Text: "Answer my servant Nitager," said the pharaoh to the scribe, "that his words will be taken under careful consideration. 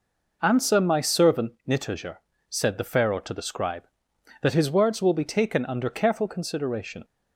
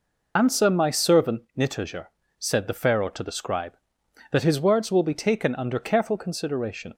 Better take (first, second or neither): first